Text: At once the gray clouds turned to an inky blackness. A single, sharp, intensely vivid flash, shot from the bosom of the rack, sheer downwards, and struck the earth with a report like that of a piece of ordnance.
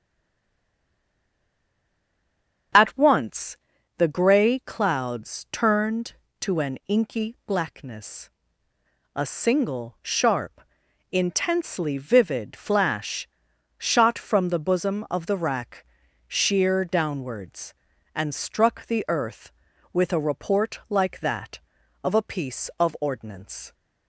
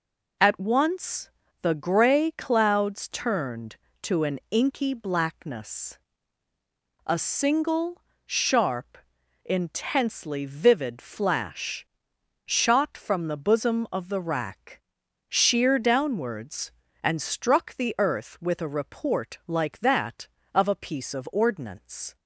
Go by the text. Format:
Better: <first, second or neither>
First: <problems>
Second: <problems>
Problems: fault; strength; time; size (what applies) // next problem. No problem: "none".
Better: second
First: stays silent before the first word; strong; until 2.7 s; 2.7 s long // starts louder than the rest; until 4.1 s; 6.5 dB // pauses between "once" and "the"; at 3.5 s; 0.42 s long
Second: pauses between "once" and "the"; slight; at 1.3 s; 0.32 s long